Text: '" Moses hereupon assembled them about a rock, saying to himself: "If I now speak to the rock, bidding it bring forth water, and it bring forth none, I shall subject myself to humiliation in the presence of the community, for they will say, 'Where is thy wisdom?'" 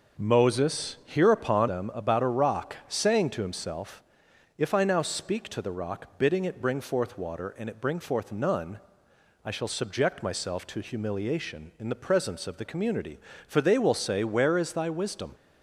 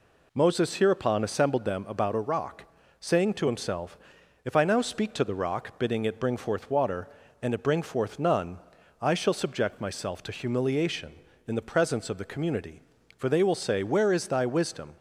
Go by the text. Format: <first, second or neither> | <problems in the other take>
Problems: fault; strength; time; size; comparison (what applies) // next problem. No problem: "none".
second | skips "assembled"; at 1.6 s